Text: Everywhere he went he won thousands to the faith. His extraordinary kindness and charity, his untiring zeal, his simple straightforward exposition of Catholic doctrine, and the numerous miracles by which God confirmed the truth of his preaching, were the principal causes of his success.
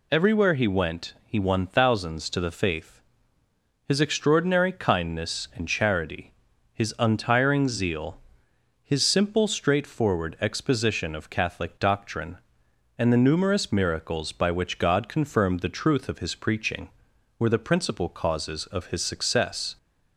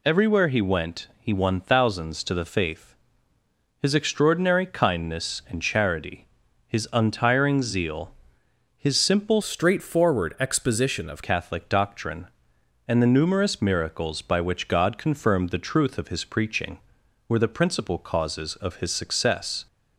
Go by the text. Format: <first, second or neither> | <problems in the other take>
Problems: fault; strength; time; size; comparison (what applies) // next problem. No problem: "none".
first | changes voice from "straightforward" to "of"; from 9.4 to 11.2 s; 1.8 s long